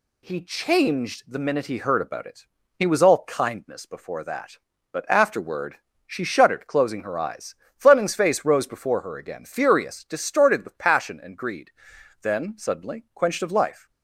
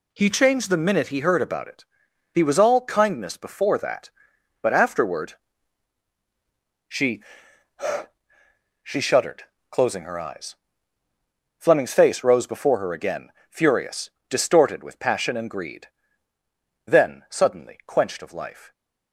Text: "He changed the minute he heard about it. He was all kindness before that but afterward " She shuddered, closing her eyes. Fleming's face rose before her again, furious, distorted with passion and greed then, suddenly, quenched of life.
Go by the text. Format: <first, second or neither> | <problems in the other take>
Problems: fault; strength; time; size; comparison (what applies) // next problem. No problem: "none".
first | says "She" twice; at 8.8 s // pauses between "greed" and "then"; at 15.8 s; 1.0 s long; noticeable in the first